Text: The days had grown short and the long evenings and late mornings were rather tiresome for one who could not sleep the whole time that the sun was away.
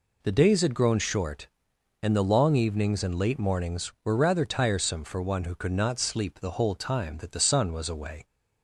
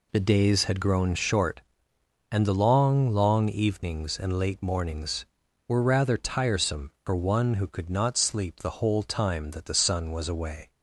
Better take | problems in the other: first | says "long" twice; at 3.1 s

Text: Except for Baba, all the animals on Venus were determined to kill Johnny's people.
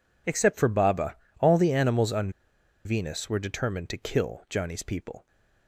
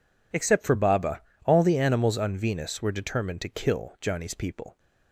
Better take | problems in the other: second | pauses between "on" and "Venus"; noticeable; at 2.3 s; 0.55 s long

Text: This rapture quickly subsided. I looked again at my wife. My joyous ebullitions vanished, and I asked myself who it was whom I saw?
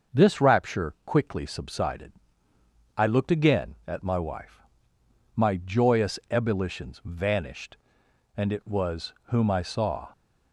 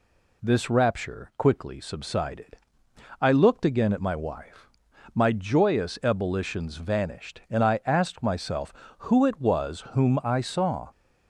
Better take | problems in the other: second | starts louder than the rest; until 1.2 s; 6 dB // skips "I asked myself who"; at 8.5 s

